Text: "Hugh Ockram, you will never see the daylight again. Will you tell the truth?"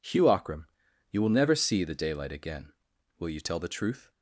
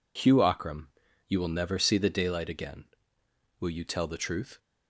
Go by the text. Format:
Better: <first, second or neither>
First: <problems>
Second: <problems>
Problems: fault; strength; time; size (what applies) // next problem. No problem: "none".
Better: neither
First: none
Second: none